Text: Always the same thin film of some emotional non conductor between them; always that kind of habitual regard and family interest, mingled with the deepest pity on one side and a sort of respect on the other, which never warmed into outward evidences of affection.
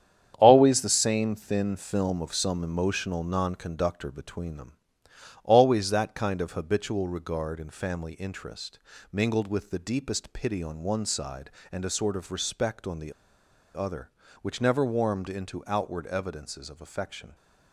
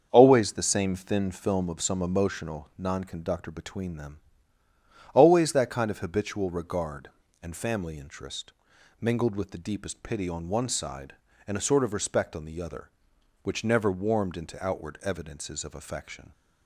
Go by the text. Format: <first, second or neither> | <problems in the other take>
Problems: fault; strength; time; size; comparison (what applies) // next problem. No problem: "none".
second | starts louder than the rest; strong; until 1.4 s; 9 dB; also in the second // pauses between "the" and "other"; noticeable; at 13.1 s; 0.62 s long